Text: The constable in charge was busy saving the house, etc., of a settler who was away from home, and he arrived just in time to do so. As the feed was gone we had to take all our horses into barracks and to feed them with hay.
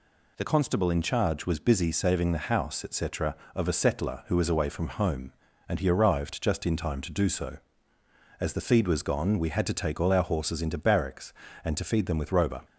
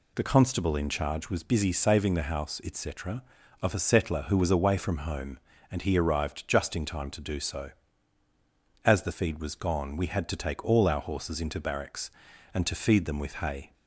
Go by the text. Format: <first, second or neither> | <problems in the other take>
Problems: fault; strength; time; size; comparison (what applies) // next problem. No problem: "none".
second | says "roba" for "hay"; at 12.3 s